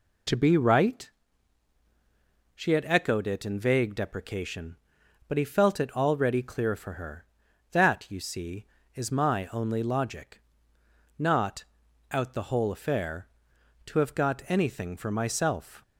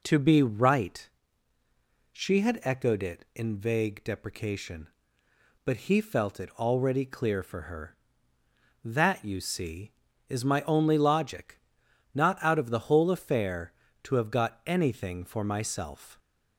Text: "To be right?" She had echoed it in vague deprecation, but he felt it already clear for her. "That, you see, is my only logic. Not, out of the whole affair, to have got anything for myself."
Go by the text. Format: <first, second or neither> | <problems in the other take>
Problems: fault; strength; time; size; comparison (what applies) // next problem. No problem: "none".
second | skips "of"; at 12.3 s